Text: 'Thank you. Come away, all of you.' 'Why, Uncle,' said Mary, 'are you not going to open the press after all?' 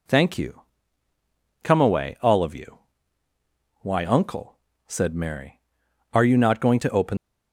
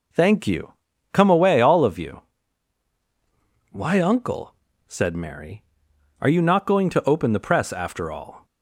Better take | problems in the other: second | stops before "the press after all"; at 7.1 s

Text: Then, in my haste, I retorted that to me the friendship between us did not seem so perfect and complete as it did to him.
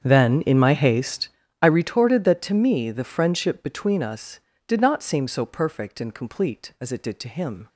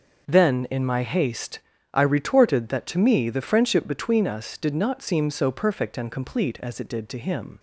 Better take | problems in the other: second | starts louder than the rest; strong; until 1.5 s; 7.5 dB

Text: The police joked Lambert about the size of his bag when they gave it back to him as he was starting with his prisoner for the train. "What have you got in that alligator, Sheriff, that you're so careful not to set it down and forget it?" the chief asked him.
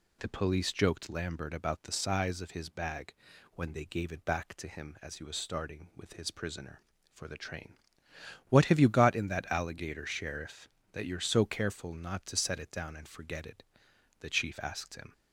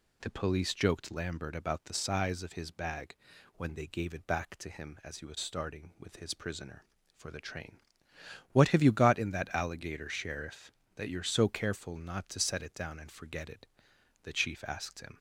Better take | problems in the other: neither | pauses between "bag" and "when"; the same in both

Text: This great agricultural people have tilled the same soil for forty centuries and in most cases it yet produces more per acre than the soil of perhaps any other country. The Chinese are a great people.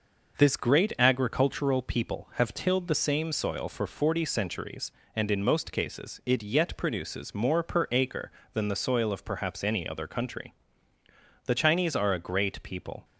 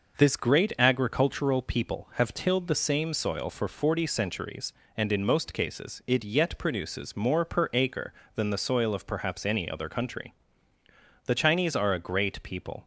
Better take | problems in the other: neither | none

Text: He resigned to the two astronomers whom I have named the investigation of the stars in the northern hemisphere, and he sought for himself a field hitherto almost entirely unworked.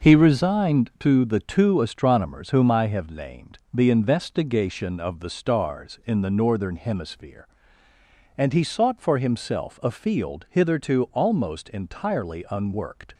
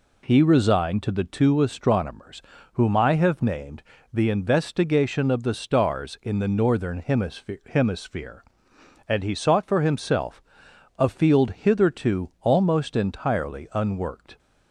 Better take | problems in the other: first | pauses between "astronomers" and "whom"; slight; at 2.4 s; 0.34 s long // pauses between "named" and "the"; slight; at 3.8 s; 0.30 s long // says "hemisphere" twice; at 7.6 s // pauses between "himself" and "a"; noticeable; at 10.4 s; 0.56 s long

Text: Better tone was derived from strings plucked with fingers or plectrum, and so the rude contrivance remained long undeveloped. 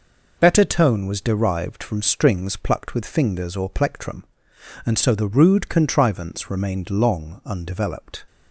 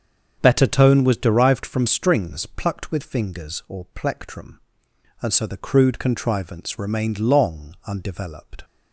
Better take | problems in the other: first | starts louder than the rest; strong; until 1.4 s; 7.5 dB // says "crude" for "rude"; at 5.5 s

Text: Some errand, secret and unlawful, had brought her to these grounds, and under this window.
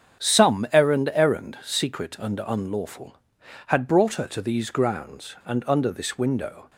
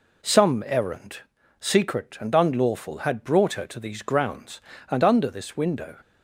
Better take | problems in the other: second | starts louder than the rest; strong; until 1.2 s; 8 dB // says "errand" twice; at 1.1 s

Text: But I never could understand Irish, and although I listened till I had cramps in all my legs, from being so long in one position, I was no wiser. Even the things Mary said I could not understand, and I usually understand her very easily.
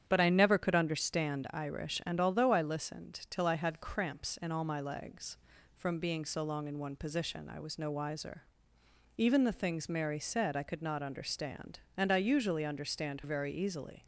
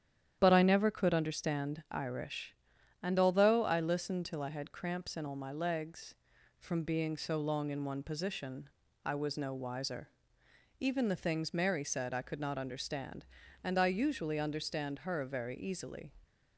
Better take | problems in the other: second | starts louder than the rest; strong; until 1.0 s; 9 dB; strong in the second // skips "her"; at 13.2 s

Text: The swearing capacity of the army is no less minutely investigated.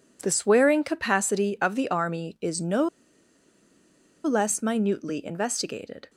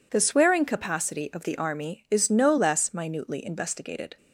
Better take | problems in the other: second | pauses between "no" and "less"; strong; at 2.8 s; 1.4 s long

